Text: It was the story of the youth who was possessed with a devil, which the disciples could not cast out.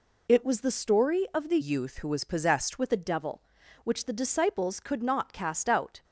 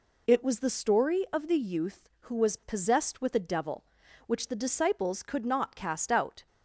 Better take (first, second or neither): second